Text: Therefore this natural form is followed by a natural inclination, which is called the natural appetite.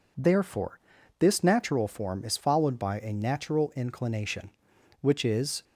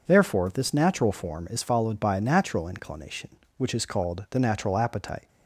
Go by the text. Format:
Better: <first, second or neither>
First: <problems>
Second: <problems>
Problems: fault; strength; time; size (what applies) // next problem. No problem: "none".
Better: second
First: pauses between "Therefore" and "this"; at 0.7 s; 0.40 s long // stops before "called the natural appetite"; at 5.6 s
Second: none